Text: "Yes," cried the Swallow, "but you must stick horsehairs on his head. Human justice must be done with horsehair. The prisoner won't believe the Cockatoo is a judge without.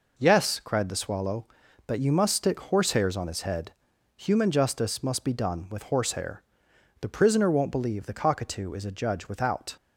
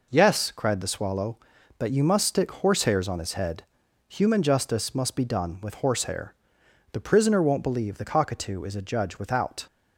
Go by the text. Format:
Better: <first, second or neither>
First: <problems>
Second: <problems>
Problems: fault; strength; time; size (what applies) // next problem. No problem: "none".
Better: neither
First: none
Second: none